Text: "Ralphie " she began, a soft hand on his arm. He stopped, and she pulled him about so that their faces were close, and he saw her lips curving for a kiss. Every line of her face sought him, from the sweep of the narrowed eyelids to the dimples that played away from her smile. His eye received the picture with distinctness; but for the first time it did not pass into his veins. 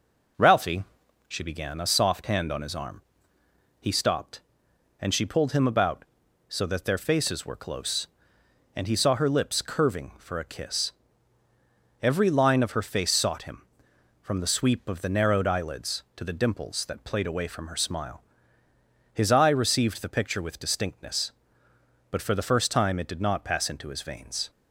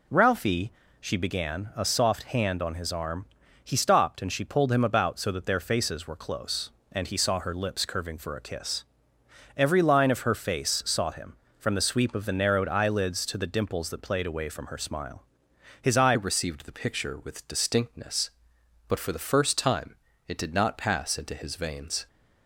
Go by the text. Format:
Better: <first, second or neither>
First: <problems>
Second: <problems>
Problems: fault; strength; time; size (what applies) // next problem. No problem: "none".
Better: first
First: none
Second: changes voice at "received"; from 16.1 s on; 5.9 s long // pauses between "time" and "it"; slight; at 19.9 s; 0.30 s long